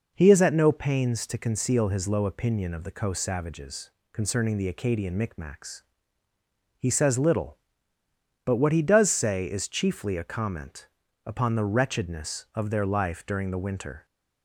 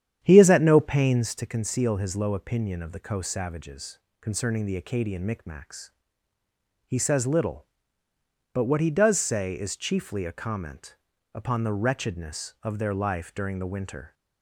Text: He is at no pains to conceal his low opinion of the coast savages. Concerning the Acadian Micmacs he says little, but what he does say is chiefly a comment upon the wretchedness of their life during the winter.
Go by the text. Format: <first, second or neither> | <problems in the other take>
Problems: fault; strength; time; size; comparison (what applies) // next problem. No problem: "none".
first | starts louder than the rest; strong; until 1.4 s; 9.5 dB // pauses between "Micmacs" and "he"; noticeable; at 5.8 s; 0.96 s long; noticeable in the first // pauses between "comment" and "upon"; at 10.9 s; 0.38 s long; also in the first